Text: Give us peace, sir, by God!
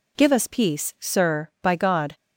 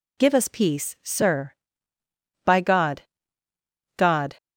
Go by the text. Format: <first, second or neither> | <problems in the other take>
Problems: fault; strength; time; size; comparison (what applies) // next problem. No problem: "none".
first | says "God" twice; at 3.9 s